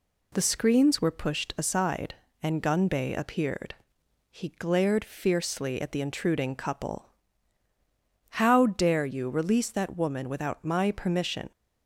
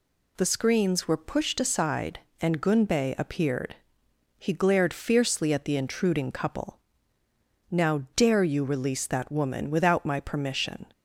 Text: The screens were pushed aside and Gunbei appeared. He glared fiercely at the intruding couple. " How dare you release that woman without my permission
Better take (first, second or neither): first